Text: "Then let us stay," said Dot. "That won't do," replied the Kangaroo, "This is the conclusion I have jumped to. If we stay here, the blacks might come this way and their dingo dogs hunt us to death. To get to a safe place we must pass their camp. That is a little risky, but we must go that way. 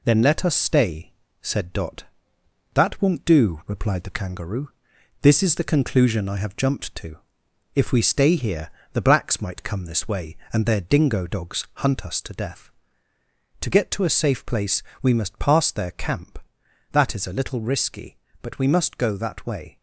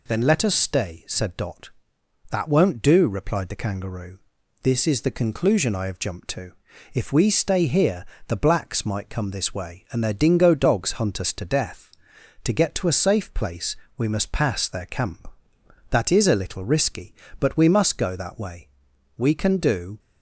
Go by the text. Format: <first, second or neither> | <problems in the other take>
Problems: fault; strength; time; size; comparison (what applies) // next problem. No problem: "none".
first | pauses between "place" and "we"; slight; at 13.7 s; 0.20 s long; slight in the first // goes on to say "We can do"; noticeable; from 19.1 s on; 0.82 s long